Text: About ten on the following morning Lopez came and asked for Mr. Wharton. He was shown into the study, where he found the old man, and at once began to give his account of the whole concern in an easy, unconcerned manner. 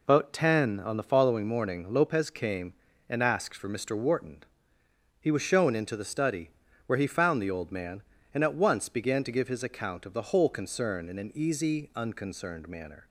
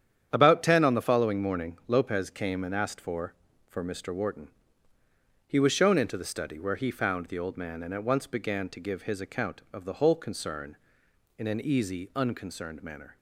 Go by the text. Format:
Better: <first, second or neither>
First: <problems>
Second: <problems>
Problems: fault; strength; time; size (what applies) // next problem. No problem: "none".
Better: first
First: none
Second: starts louder than the rest; strong; until 1.3 s; 9.5 dB // says "for" twice; at 3.6 s